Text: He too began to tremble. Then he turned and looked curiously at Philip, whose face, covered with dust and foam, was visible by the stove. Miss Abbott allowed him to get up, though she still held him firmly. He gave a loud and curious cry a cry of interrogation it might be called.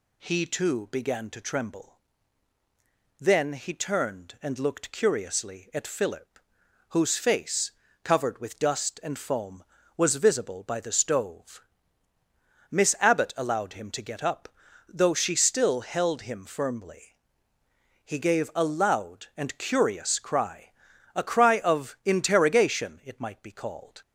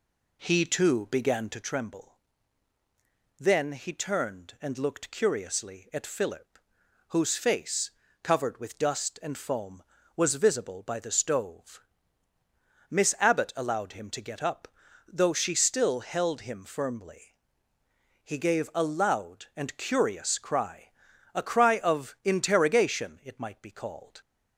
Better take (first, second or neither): first